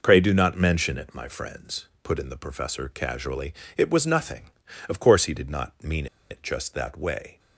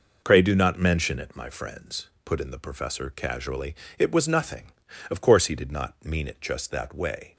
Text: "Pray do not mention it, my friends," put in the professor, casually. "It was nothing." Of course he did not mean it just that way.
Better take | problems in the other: second | pauses between "mean" and "it"; slight; at 6.0 s; 0.23 s long

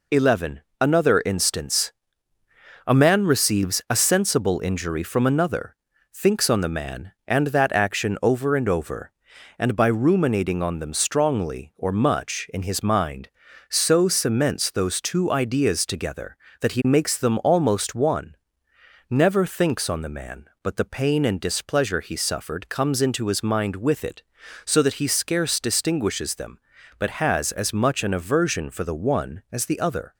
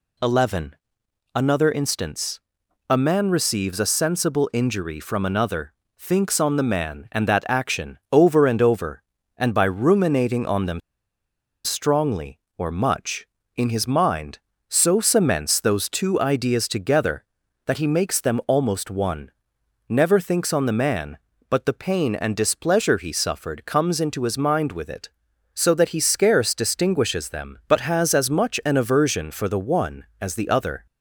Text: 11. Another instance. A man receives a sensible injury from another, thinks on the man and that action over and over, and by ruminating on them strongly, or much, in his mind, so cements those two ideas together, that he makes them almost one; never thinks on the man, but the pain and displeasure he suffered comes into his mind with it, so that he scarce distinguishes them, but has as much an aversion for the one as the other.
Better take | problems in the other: first | pauses between "them" and "strongly"; noticeable; at 10.7 s; 0.85 s long

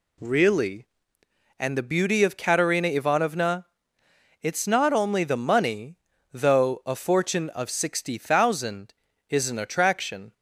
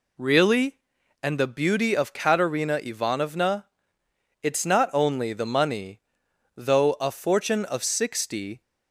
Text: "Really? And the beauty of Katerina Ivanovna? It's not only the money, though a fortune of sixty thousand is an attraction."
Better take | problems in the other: first | stops before "thousand is an attraction"; at 8.6 s

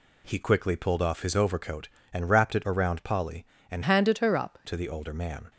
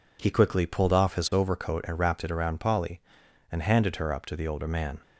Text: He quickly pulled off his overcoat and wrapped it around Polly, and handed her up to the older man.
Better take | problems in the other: second | changes voice from "handed" to "up"; from 3.8 to 4.5 s; 0.7 s long

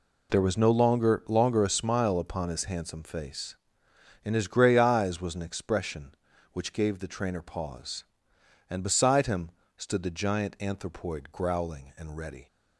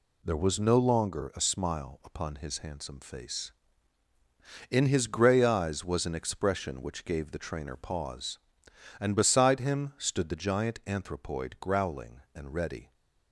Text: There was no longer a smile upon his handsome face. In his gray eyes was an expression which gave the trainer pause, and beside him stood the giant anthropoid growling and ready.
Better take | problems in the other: second | says "longer" twice; at 1.2 s // pauses between "him" and "stood"; slight; at 9.5 s; 0.26 s long

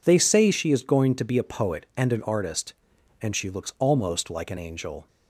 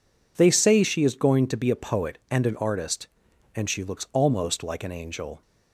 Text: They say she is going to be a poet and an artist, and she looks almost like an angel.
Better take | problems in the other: neither | none

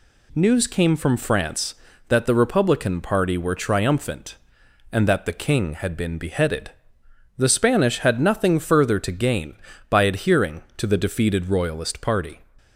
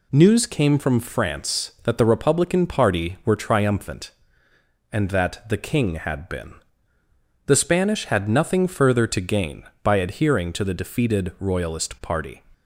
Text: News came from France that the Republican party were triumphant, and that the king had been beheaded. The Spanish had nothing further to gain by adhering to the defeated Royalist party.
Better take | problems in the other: first | skips "beheaded"; at 6.9 s

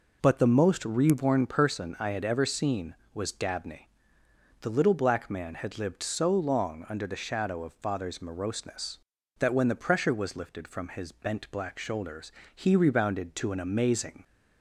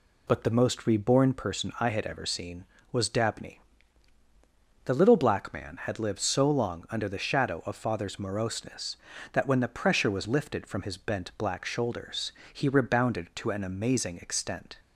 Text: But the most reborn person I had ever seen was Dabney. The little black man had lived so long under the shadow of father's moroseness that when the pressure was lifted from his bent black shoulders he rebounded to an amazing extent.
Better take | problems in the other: second | pauses between "shoulders" and "he"; slight; at 12.2 s; 0.24 s long; slight in the second // stops before "extent"; at 14.2 s

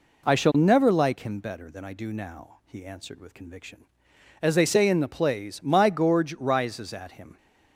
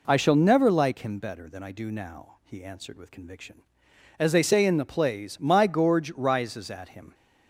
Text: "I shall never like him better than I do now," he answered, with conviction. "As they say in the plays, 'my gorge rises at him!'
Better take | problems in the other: neither | none

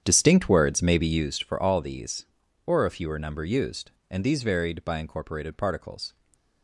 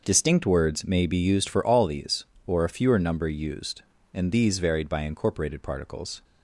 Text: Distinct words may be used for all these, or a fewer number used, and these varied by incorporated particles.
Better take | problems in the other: second | starts louder than the rest; strong; until 1.3 s; 8.5 dB // stays silent after the last word; slight; from 6.0 s on; 0.6 s long

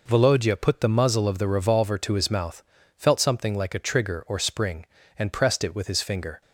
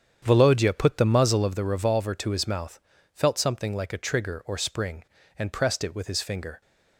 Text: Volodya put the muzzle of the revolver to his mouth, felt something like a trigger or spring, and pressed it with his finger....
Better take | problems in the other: first | starts louder than the rest; strong; until 1.6 s; 8 dB

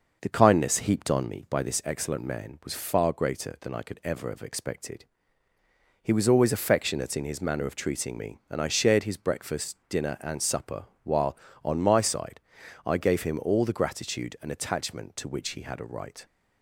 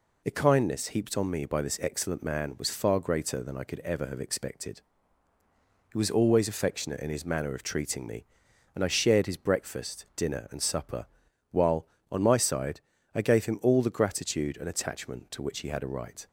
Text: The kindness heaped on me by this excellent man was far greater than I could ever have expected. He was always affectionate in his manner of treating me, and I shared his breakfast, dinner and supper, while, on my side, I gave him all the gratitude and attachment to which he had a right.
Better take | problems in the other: second | starts louder than the rest; noticeable; until 1.4 s; 6 dB

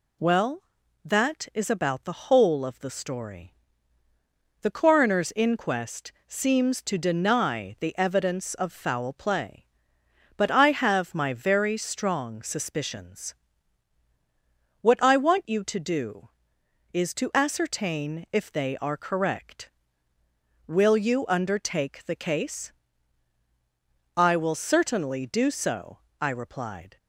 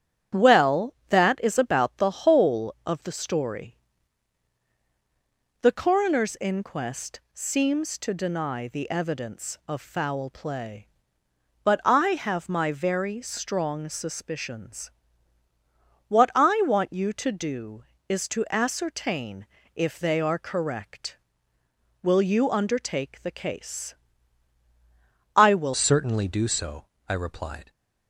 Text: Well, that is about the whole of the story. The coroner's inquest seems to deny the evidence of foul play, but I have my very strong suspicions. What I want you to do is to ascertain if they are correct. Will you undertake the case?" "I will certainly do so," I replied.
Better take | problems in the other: first | starts louder than the rest; strong; until 1.5 s; 10 dB // pauses between "inquest" and "seems"; slight; at 7.1 s; 0.16 s long; slight in the first // pauses between "ascertain" and "if"; slight; at 19.4 s; 0.30 s long // changes voice at "certainly"; from 25.7 s on; 1.9 s long

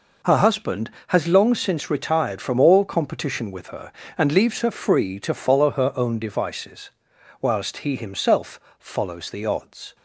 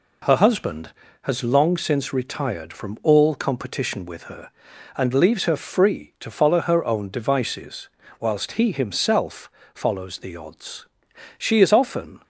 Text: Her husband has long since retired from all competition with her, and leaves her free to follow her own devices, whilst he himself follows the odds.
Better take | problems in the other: first | pauses between "himself" and "follows"; slight; at 9.5 s; 0.24 s long; slight in the first // goes on to say "She is often"; noticeable; from 11.3 s on; 0.86 s long

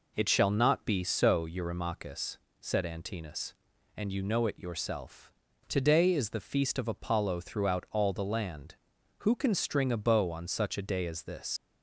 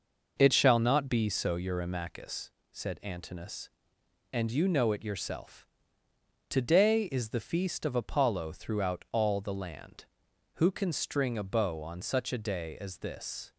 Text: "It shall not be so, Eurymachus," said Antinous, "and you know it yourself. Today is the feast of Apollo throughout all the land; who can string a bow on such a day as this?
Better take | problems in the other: second | leaves "this" unfinished; at 11.5 s; 90 ms

